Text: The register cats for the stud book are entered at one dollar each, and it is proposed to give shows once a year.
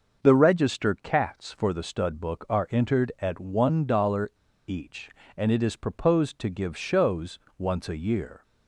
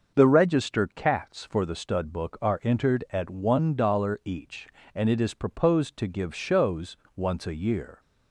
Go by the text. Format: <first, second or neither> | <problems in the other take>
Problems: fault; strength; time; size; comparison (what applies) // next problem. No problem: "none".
second | starts louder than the rest; until 1.3 s; 6 dB; also in the second // pauses between "dollar" and "each"; at 4.3 s; 0.37 s long // pauses between "shows" and "once"; slight; at 7.3 s; 0.20 s long; slight in the second